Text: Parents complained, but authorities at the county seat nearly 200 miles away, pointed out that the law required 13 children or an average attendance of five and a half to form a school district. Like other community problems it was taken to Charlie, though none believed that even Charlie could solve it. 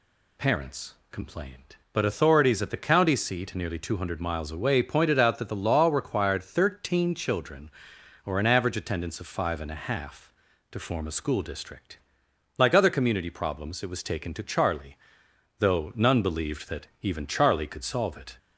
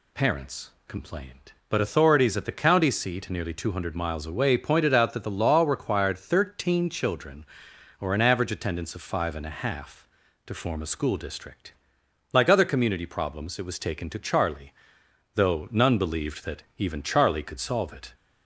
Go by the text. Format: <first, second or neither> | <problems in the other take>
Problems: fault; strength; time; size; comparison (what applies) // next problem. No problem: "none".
neither | pauses between "Parents" and "complained"; slight; the same in both